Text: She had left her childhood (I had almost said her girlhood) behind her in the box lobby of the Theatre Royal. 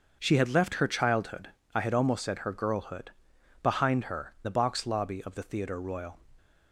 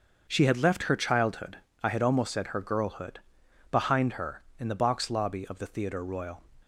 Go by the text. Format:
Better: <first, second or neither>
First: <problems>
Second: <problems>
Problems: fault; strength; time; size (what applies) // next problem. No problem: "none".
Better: second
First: starts louder than the rest; until 1.2 s; 6.5 dB // skips "in"; at 4.3 s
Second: starts louder than the rest; until 1.3 s; 6.5 dB